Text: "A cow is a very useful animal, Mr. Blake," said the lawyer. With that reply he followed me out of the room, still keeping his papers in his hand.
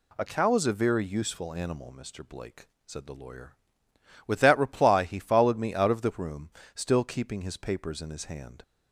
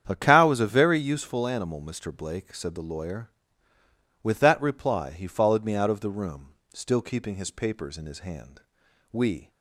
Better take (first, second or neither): first